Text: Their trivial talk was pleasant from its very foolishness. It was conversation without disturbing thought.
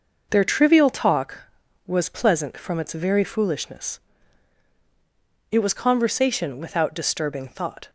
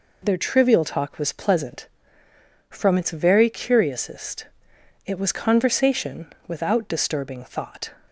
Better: first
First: none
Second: says "curiousest" for "foolishness"; at 3.4 s

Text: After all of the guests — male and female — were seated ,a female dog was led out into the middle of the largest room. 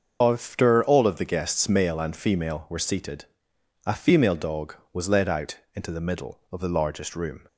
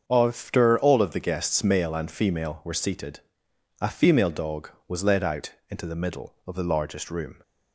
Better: second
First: loses the start of "After"; at 0.2 s; 75 ms // starts louder than the rest; until 1.2 s; 6.5 dB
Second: starts louder than the rest; until 1.0 s; 7 dB

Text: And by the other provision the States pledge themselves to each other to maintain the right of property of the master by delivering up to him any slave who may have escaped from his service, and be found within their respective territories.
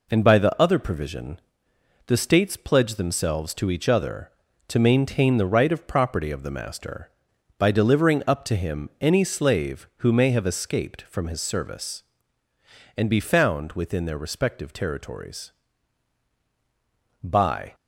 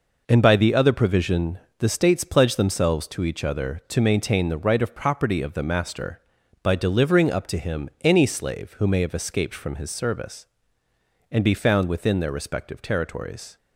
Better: second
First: pauses between "provision" and "the"; noticeable; at 1.3 s; 0.68 s long // goes on to say "By"; from 17.2 s on; 0.52 s long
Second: pauses between "provision" and "the"; slight; at 1.5 s; 0.20 s long

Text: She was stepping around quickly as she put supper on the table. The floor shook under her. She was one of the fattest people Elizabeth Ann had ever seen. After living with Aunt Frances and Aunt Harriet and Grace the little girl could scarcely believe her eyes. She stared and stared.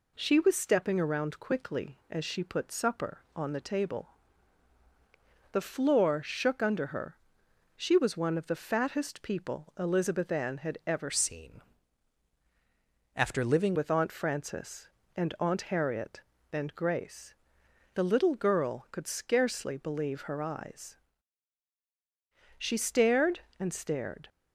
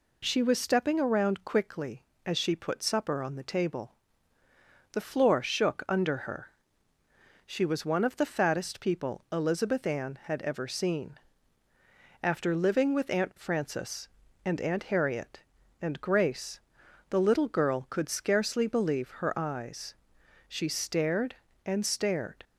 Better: second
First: changes voice from "seen" to "living"; from 11.1 to 13.7 s; 2.6 s long // pauses between "Grace" and "the"; noticeable; at 17.3 s; 0.60 s long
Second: pauses between "Grace" and "the"; noticeable; at 16.5 s; 0.50 s long

